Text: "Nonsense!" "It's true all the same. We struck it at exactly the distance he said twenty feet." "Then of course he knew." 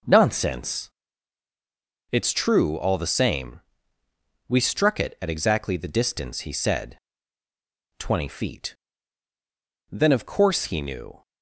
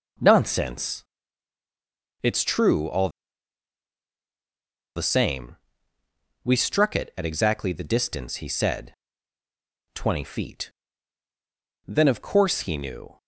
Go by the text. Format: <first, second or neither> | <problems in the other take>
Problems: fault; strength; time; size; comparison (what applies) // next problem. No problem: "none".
first | pauses between "all" and "the"; strong; at 3.0 s; 1.8 s long // pauses between "said" and "twenty"; noticeable; at 8.9 s; 0.98 s long; noticeable in the first